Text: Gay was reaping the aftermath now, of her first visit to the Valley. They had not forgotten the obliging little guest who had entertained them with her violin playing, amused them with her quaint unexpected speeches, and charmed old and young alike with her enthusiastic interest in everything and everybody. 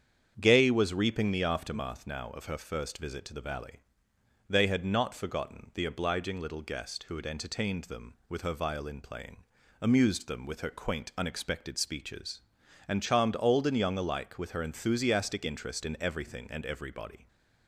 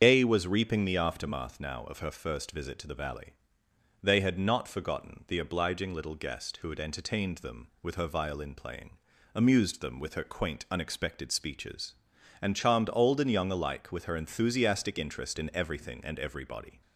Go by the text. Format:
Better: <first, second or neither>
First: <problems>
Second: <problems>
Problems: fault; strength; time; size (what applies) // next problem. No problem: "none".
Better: first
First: starts louder than the rest; strong; until 1.3 s; 8 dB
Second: loses the start of "Gay"; at 0.0 s; 115 ms // starts louder than the rest; strong; until 1.0 s; 7.5 dB